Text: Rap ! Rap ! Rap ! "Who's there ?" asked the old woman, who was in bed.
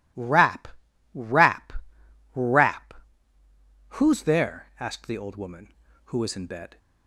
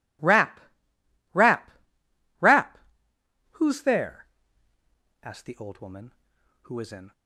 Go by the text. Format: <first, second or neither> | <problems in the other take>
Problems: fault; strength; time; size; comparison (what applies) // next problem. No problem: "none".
first | stops before "bed"; at 7.1 s